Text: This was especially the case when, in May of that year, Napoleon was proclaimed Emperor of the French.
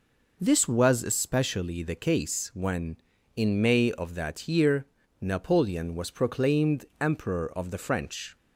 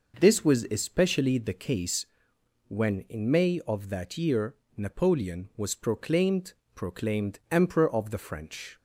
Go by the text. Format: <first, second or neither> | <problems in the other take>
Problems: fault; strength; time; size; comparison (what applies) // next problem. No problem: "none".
first | pauses between "case" and "when"; noticeable; at 2.0 s; 0.64 s long // says "proclaimed" twice; at 6.7 s